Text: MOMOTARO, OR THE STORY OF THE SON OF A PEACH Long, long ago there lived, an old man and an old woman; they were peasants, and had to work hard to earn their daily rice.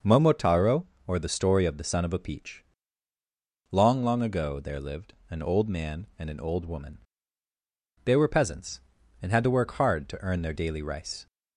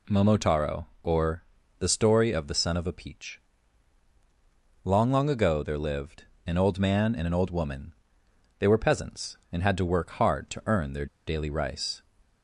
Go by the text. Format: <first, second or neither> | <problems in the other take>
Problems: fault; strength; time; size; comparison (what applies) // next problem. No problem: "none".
first | pauses between "OR" and "THE"; at 1.4 s; 0.38 s long // pauses between "PEACH" and "Long"; strong; at 3.3 s; 1.4 s long; also in the first // pauses between "their" and "daily"; slight; at 11.0 s; 0.20 s long